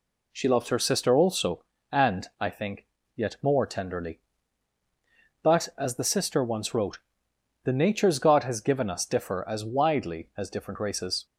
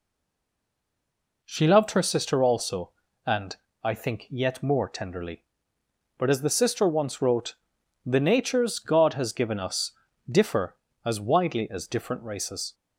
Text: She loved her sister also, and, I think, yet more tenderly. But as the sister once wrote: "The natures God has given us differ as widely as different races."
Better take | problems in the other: first | stays silent before the first word; noticeable; until 1.4 s; 1.4 s long // pauses between "us" and "differ"; at 9.8 s; 0.40 s long

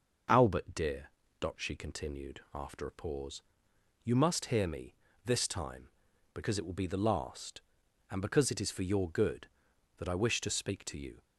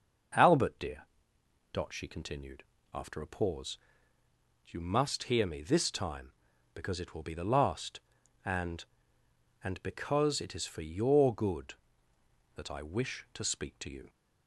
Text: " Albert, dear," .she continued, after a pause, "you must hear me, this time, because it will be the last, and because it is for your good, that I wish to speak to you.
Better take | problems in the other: first | starts louder than the rest; until 2.0 s; 6.5 dB // says "and" twice; at 9.6 s

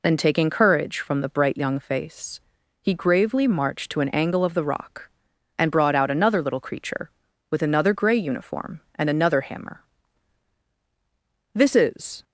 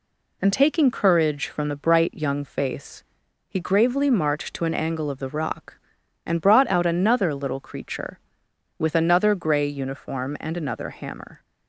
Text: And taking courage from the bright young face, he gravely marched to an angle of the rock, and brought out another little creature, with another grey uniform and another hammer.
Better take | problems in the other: second | goes on to say "This is"; noticeable; from 11.5 s on; 0.68 s long

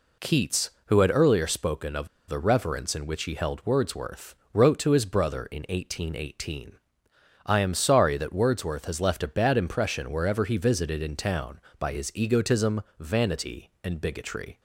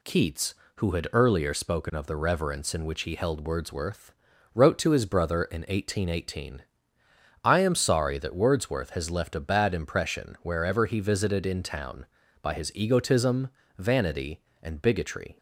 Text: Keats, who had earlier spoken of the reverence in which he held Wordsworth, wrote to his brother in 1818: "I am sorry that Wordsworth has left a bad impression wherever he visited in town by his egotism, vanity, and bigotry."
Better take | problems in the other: second | pauses between "of" and "the"; slight; at 2.0 s; 0.20 s long

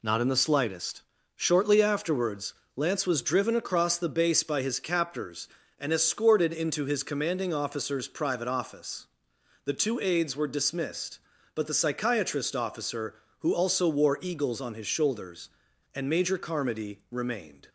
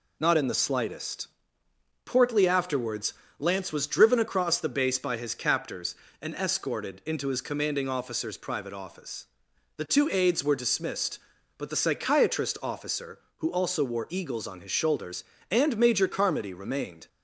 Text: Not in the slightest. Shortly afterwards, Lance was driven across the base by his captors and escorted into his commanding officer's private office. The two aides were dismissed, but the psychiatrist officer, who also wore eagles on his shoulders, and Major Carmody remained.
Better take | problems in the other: first | says "Portly" for "Shortly"; at 2.0 s

